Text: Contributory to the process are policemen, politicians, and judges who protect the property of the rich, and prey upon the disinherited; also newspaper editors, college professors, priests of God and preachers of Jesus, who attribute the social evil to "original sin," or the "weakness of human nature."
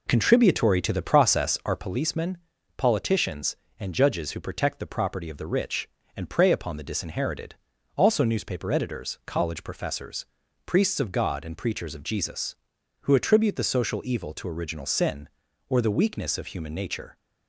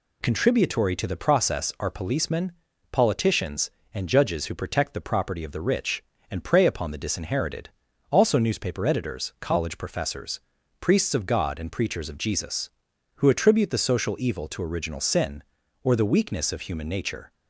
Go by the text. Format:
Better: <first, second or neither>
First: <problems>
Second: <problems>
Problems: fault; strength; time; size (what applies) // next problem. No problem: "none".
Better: second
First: starts louder than the rest; until 2.0 s; 3.5 dB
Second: none